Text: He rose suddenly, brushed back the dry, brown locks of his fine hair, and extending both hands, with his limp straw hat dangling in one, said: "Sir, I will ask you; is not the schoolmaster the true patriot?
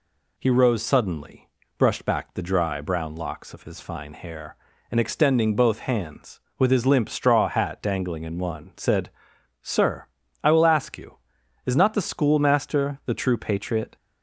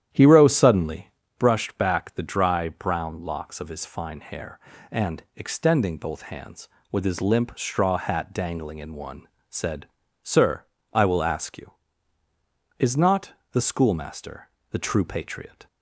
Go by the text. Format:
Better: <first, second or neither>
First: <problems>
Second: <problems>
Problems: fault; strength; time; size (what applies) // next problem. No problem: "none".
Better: first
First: none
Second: starts louder than the rest; strong; until 1.3 s; 10.5 dB // pauses between "not" and "the"; slight; at 13.3 s; 0.22 s long // pauses between "schoolmaster" and "the"; slight; at 14.4 s; 0.22 s long